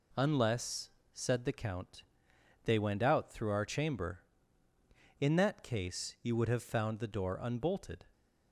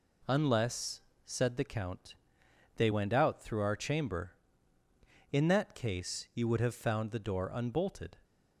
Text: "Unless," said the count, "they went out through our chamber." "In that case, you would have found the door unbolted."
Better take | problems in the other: neither | none

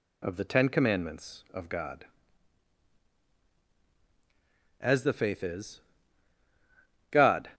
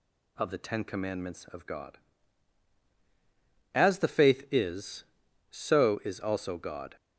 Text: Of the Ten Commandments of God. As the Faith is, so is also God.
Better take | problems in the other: second | skips "so is also"; at 6.4 s

